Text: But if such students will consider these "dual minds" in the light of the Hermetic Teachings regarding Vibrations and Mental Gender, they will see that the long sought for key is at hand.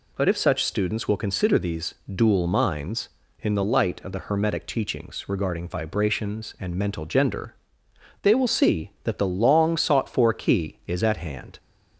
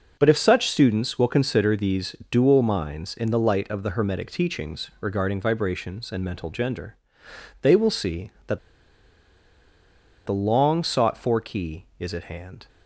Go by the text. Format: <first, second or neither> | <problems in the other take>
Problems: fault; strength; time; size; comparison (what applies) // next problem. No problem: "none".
first | pauses between "these" and "dual"; slight; at 2.1 s; 0.16 s long; slight in the first // pauses between "that" and "the"; strong; at 8.5 s; 1.6 s long